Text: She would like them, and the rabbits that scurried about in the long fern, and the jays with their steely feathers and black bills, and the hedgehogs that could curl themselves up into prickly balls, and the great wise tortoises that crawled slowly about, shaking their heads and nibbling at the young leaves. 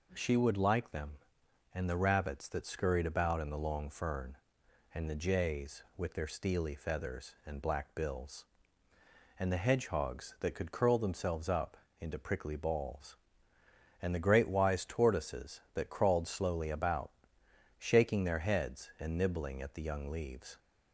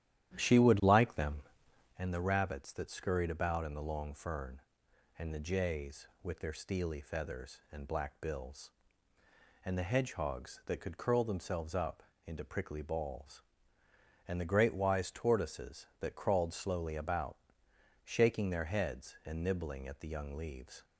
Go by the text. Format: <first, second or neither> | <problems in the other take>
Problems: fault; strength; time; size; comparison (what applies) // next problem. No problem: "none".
first | starts louder than the rest; strong; until 2.1 s; 11.5 dB // pauses between "up" and "into"; slight; at 12.0 s; 0.24 s long; slight in the first